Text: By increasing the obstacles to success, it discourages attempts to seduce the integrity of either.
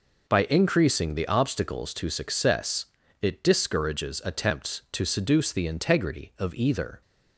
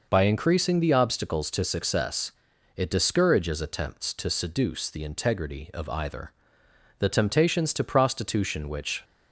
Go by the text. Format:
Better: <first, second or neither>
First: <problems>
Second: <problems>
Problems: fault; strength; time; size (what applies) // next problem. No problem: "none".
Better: first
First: none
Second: goes on to say "The temptations to prostitution which"; strong; from 6.9 s on; 2.0 s long